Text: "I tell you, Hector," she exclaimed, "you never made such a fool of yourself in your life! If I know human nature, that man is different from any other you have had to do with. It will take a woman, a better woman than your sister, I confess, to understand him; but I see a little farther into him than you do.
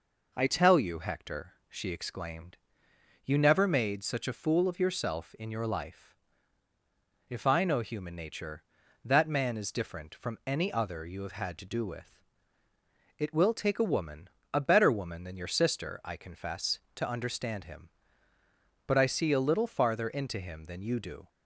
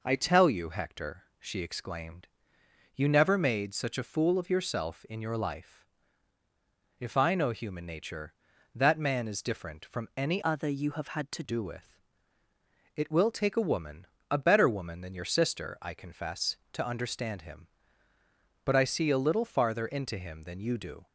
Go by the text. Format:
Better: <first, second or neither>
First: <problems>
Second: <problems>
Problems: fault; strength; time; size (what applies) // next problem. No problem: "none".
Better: first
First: none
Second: changes voice from "other" to "to"; from 10.4 to 11.4 s; 1.0 s long